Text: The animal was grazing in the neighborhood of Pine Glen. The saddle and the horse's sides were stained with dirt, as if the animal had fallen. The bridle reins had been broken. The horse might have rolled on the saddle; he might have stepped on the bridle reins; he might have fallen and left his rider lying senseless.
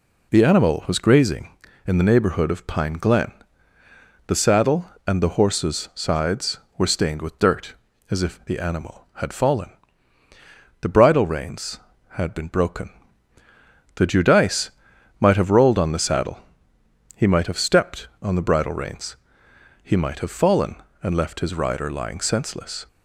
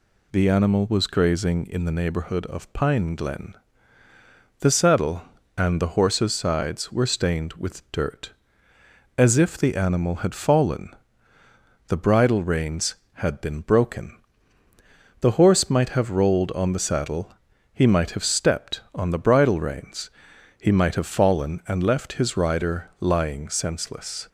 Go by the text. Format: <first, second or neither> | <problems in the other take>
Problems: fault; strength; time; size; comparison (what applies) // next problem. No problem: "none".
second | says "judice" for "horse"; at 14.0 s